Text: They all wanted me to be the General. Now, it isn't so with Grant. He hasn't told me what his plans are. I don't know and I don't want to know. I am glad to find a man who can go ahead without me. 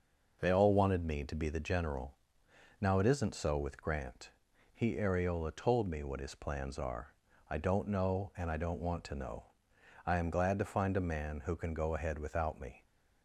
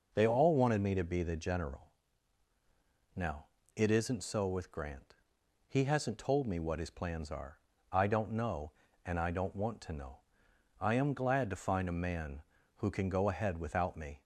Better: second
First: says "areola" for "hasn't"; at 4.9 s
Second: none

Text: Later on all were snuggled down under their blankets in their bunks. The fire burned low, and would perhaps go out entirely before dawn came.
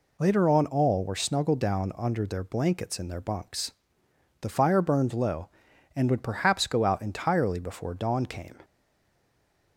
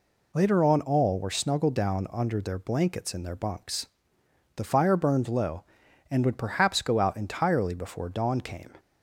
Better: second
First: stays silent after the last word; from 8.6 s on; 1.1 s long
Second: none

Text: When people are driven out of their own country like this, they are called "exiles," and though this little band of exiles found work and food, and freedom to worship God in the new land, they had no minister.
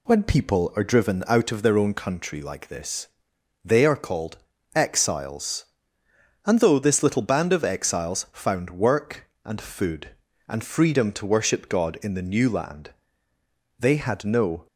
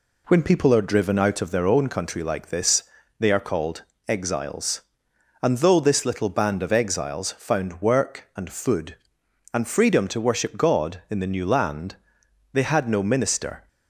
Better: second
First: pauses between "called" and "exiles"; slight; at 4.3 s; 0.36 s long // stops before "minister"; at 14.6 s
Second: pauses between "called" and "exiles"; slight; at 3.8 s; 0.24 s long

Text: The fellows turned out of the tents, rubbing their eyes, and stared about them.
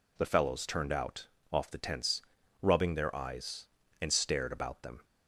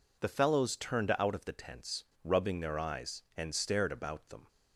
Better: second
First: says "off" for "of"; at 1.5 s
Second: none

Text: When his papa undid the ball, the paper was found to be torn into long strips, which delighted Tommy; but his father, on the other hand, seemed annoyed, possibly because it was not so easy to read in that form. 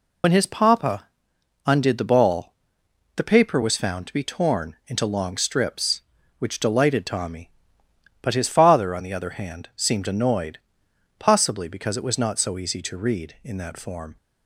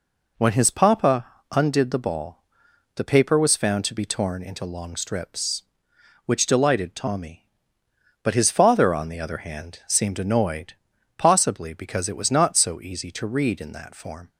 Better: second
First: loses the start of "When"; at 0.2 s; 55 ms // pauses between "papa" and "undid"; noticeable; at 1.0 s; 0.58 s long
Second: pauses between "papa" and "undid"; slight; at 1.2 s; 0.26 s long

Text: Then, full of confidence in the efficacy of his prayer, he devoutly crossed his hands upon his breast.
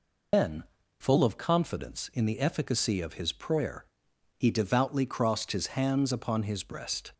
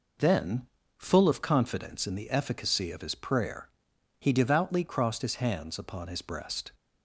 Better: second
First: loses the start of "Then"; at 0.3 s; 140 ms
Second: none

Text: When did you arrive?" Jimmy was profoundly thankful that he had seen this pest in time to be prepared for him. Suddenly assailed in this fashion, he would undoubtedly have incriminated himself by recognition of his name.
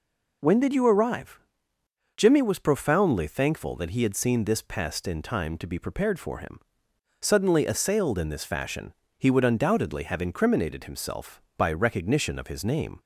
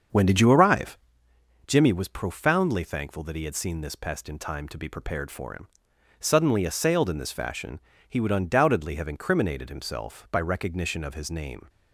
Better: first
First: none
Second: starts louder than the rest; until 1.3 s; 7 dB

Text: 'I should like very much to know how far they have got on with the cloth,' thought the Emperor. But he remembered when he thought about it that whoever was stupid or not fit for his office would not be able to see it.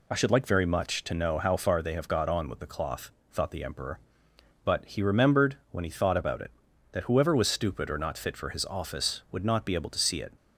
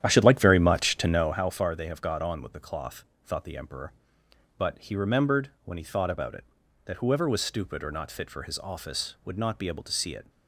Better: first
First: none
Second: starts louder than the rest; strong; until 1.4 s; 10.5 dB

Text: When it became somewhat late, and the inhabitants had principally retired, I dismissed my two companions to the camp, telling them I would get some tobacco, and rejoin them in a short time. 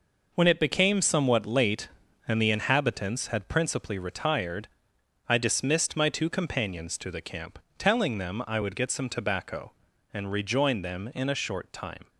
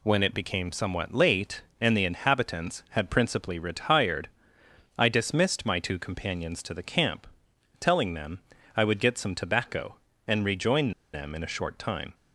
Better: first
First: none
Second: pauses between "them" and "I"; slight; at 8.3 s; 0.36 s long // pauses between "rejoin" and "them"; slight; at 10.9 s; 0.22 s long

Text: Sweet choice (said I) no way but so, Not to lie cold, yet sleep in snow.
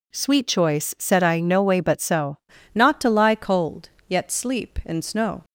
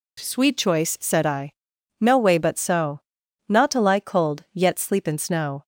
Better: second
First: changes voice at "Not"; from 2.7 s on; 2.7 s long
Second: none

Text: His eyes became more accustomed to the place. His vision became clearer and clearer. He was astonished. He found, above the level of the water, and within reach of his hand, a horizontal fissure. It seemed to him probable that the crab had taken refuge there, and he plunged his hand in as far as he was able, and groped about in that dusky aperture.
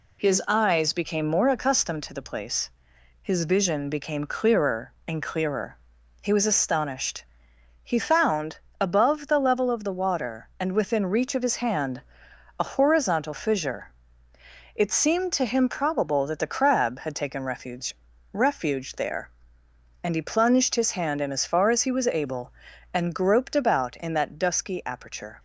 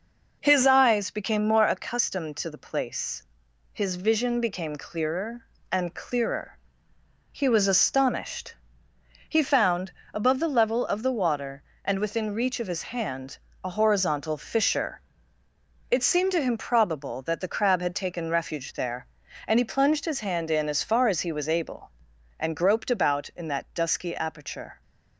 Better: second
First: says "refuge" twice; at 18.3 s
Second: none

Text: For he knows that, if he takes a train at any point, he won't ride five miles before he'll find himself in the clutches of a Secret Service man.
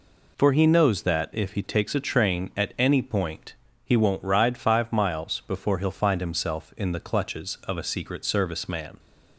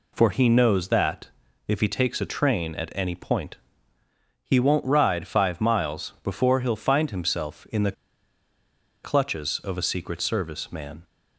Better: first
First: none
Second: pauses between "the" and "clutches"; at 7.9 s; 1.1 s long

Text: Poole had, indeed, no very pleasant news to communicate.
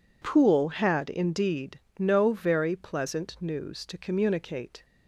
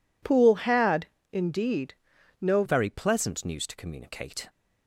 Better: first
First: none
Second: changes voice at "very"; from 2.6 s on; 1.8 s long

